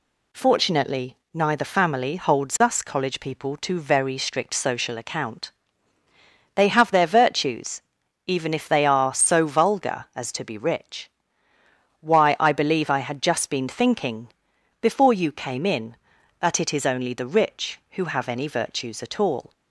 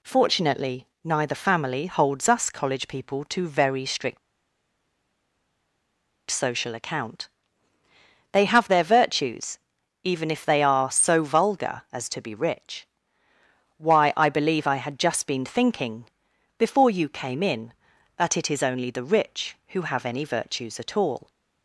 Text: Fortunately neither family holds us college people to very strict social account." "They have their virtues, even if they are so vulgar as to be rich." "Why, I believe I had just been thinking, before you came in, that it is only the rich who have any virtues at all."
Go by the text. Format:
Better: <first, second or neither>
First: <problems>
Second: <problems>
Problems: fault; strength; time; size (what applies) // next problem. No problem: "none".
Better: first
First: pauses between "Fortunately" and "neither"; slight; at 1.1 s; 0.18 s long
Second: pauses between "Fortunately" and "neither"; slight; at 0.8 s; 0.18 s long // pauses between "strict" and "social"; strong; at 4.1 s; 2.1 s long